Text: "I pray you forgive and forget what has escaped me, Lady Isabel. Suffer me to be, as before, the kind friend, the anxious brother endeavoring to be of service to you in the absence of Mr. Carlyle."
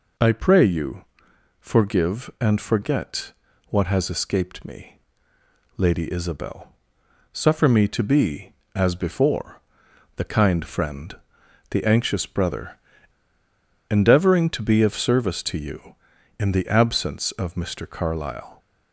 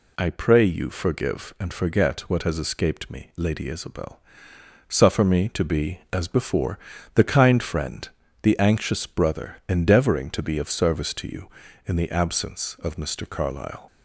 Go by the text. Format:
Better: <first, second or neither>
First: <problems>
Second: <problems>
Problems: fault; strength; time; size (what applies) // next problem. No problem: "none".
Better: second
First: pauses between "you" and "forgive"; noticeable; at 1.0 s; 0.54 s long // pauses between "forget" and "what"; slight; at 3.3 s; 0.36 s long // pauses between "brother" and "endeavoring"; at 12.7 s; 1.0 s long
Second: none